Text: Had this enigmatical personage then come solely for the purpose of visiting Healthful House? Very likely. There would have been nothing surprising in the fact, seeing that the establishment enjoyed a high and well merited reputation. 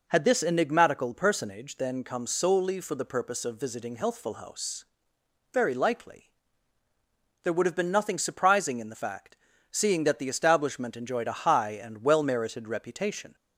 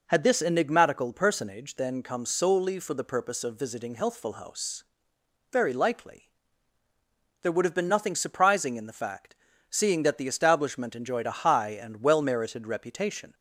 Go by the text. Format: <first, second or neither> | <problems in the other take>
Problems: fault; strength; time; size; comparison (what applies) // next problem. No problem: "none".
neither | none